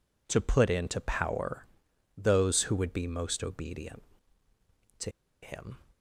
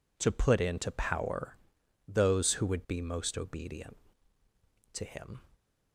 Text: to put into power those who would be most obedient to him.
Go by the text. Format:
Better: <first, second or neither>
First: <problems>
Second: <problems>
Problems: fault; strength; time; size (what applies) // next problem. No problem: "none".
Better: second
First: pauses between "power" and "those"; noticeable; at 1.6 s; 0.52 s long // pauses between "to" and "him"; slight; at 5.0 s; 0.33 s long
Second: pauses between "power" and "those"; noticeable; at 1.5 s; 0.52 s long